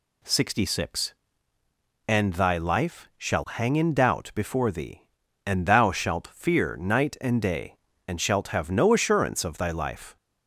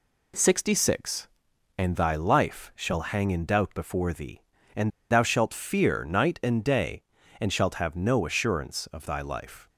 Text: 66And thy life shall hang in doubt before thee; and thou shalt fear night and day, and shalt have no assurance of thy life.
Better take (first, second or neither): first